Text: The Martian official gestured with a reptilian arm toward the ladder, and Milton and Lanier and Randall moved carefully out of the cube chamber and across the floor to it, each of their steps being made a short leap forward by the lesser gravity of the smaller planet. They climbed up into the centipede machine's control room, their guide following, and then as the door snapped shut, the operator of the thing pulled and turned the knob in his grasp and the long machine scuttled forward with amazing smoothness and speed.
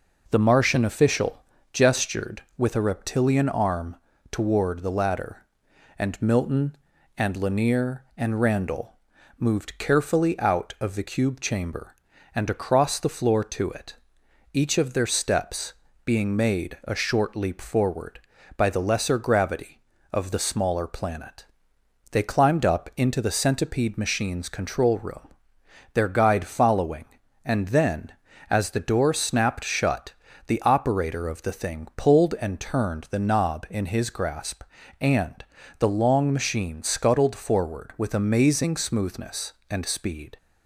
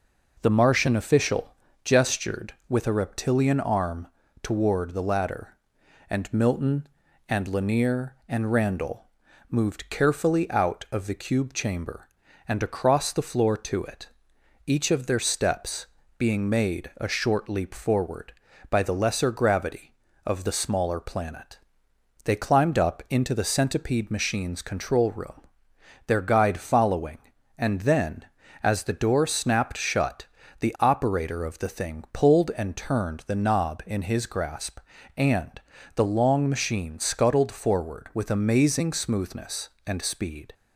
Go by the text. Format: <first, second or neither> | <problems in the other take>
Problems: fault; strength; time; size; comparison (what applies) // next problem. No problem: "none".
neither | pauses between "official" and "gestured"; slight; the same in both // pauses between "arm" and "toward"; the same in both // pauses between "Randall" and "moved"; the same in both // pauses between "steps" and "being"; slight; the same in both // pauses between "and" and "the"; slight; the same in both